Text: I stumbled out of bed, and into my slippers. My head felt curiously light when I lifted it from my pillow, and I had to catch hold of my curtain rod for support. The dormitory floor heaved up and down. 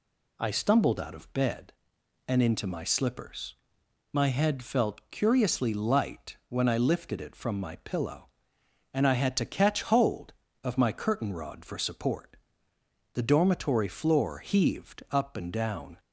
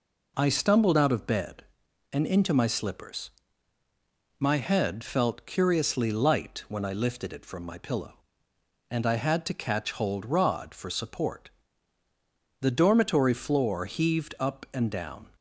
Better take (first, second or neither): first